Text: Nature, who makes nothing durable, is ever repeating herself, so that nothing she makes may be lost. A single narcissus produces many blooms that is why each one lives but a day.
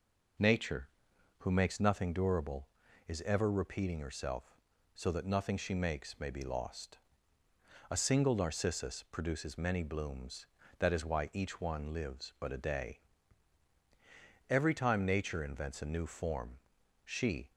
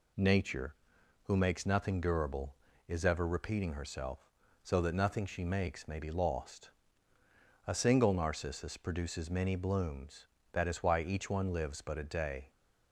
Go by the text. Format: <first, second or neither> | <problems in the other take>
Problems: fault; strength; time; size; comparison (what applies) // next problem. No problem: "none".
second | goes on to say "Every time Nature invents a new form she"; strong; from 14.4 s on; 3.0 s long